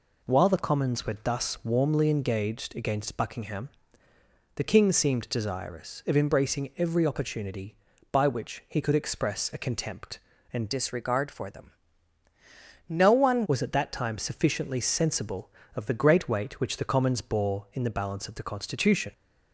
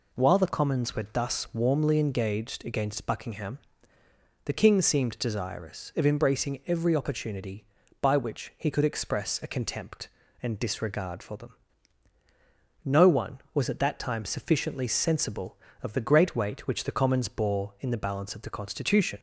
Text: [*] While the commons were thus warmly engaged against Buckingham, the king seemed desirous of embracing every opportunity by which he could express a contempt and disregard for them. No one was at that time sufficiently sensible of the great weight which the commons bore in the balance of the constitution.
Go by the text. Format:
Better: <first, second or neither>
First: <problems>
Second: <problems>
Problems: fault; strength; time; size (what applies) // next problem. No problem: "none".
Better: second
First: changes voice from "disregard" to "one"; from 10.7 to 13.4 s; 2.7 s long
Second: none